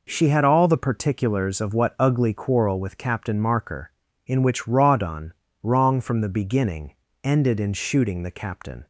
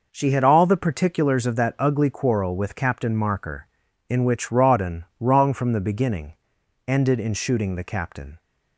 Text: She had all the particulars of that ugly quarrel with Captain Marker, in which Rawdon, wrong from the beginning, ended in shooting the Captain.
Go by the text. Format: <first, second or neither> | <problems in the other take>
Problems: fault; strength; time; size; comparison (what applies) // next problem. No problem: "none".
second | says "what" for "that"; at 1.7 s